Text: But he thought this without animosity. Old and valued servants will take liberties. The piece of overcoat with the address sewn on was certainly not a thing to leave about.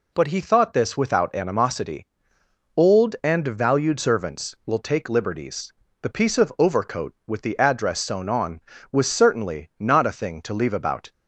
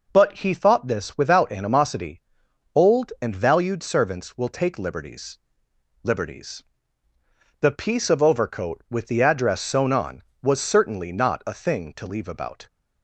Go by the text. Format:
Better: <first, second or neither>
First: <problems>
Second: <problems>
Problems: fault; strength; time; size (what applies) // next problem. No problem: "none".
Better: first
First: none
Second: says "liberties" twice; at 6.0 s